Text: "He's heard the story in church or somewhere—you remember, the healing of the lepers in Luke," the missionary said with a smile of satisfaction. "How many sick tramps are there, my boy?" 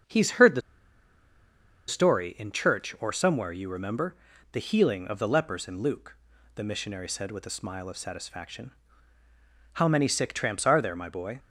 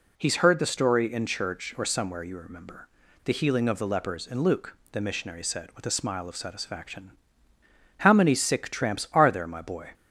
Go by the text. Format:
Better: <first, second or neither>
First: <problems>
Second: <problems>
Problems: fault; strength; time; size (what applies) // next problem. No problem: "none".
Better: second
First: starts louder than the rest; until 2.3 s; 7 dB // pauses between "the" and "story"; strong; at 0.6 s; 1.2 s long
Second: none